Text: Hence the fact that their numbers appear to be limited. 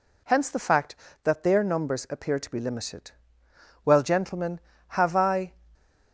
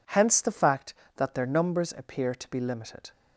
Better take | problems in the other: second | goes on to say "Well gentlemen have I"; strong; from 3.8 s on; 1.7 s long

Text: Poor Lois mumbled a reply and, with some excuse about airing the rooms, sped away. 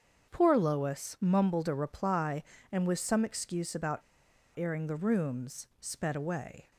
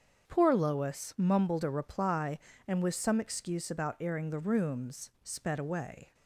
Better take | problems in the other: second | starts louder than the rest; strong; until 1.3 s; 7 dB; strong in the second // pauses between "about" and "airing"; noticeable; at 4.0 s; 0.56 s long

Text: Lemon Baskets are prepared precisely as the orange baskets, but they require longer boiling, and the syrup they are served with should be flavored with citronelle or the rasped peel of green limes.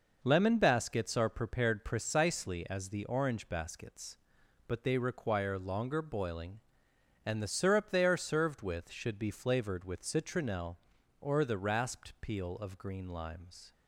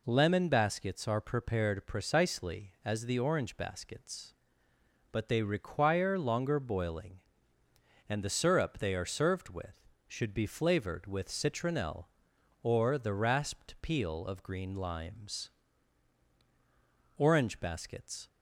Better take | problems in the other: first | goes on to say "Orange Baskets"; noticeable; from 17.1 s on; 1.1 s long

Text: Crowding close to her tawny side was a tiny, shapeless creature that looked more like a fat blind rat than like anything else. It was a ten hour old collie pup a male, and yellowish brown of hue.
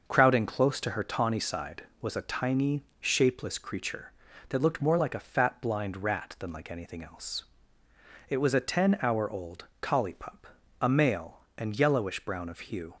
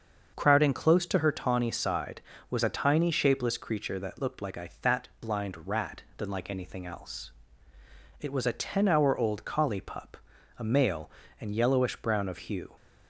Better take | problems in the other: first | starts louder than the rest; until 1.3 s; 6.5 dB; also in the first // skips "more"; at 4.4 s // pauses between "pup" and "a"; at 10.1 s; 0.42 s long; slight in the first

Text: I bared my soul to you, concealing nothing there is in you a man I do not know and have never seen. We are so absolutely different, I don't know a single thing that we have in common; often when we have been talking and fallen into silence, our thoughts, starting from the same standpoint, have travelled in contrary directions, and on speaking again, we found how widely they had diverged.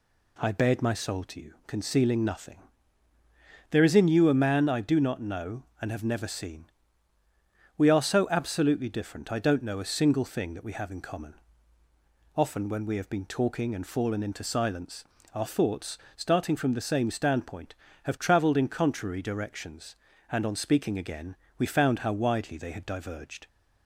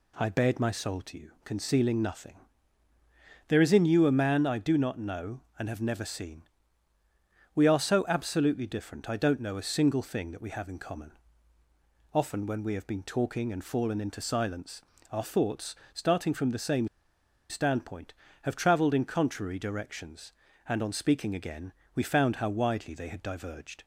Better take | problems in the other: first | pauses between "nothing" and "there"; at 2.3 s; 1.1 s long; also in the first // pauses between "same" and "standpoint"; noticeable; at 16.8 s; 0.61 s long

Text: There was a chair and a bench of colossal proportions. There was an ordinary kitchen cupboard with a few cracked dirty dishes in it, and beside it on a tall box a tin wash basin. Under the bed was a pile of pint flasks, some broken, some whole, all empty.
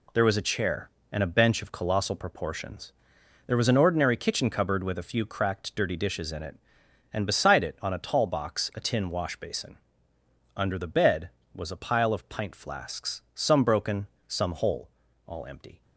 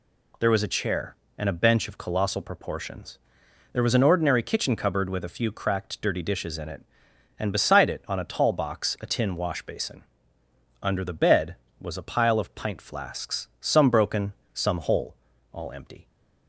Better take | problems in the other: second | gets quieter; strong; throughout; 7.5 dB

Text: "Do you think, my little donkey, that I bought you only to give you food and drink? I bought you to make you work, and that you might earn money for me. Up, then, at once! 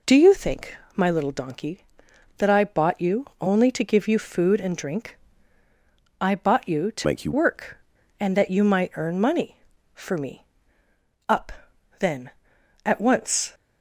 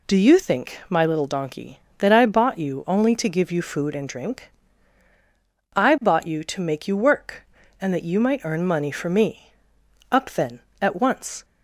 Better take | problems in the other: second | pauses between "you" and "only"; slight; at 3.2 s; 0.16 s long // changes voice from "make" to "you"; from 7.0 to 7.3 s; 0.3 s long

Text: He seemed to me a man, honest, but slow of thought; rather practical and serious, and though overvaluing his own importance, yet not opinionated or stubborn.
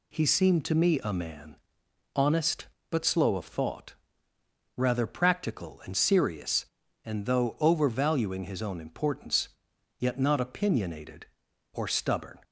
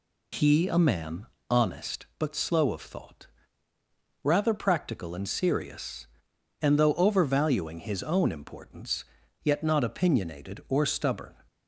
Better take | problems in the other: first | skips "seemed to me"; at 0.6 s

